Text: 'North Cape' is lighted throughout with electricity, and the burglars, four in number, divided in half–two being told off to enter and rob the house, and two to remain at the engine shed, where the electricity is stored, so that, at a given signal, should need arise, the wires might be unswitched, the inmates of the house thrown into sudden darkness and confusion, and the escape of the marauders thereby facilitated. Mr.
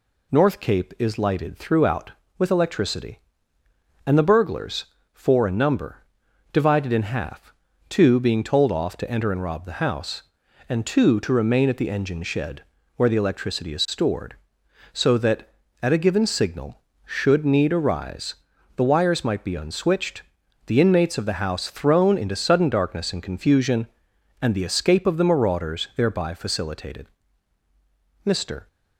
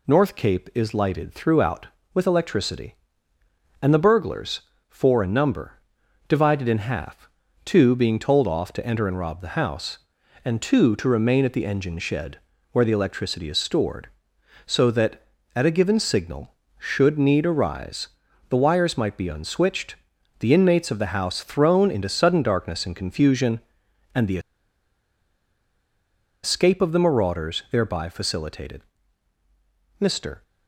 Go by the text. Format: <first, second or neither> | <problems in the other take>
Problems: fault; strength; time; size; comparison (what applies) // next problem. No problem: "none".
first | pauses between "the" and "escape"; strong; at 24.3 s; 2.0 s long